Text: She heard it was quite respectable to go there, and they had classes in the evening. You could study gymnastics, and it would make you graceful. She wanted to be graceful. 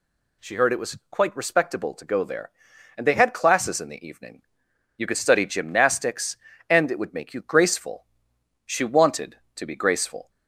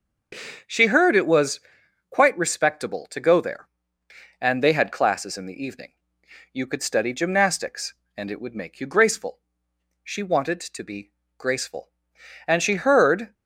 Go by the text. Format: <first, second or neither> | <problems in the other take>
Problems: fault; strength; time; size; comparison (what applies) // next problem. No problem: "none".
first | starts louder than the rest; noticeable; until 2.1 s; 6 dB // pauses between "was" and "quite"; noticeable; at 1.5 s; 0.50 s long // pauses between "be" and "graceful"; slight; at 11.1 s; 0.28 s long // goes on to say "And she heard"; noticeable; from 12.4 s on; 0.86 s long